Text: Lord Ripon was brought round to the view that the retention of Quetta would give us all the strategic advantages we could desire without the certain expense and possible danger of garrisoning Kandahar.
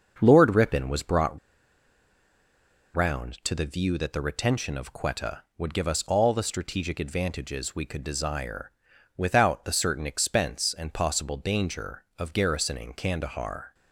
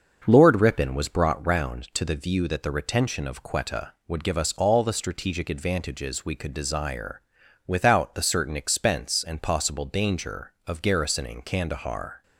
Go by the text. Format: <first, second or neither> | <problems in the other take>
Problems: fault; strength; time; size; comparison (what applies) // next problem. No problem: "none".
second | starts louder than the rest; noticeable; until 1.1 s; 6 dB; noticeable in the second // pauses between "brought" and "round"; strong; at 1.3 s; 1.5 s long // pauses between "desire" and "without"; at 8.7 s; 0.44 s long; also in the second